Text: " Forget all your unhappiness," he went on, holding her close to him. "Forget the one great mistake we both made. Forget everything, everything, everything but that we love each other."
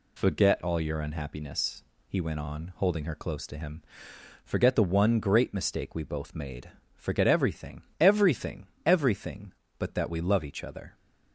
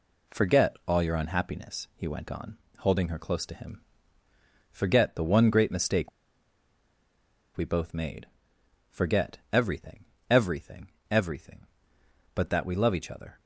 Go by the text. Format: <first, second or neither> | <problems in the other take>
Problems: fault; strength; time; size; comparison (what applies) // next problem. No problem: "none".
first | pauses between "mistake" and "we"; strong; at 6.1 s; 1.4 s long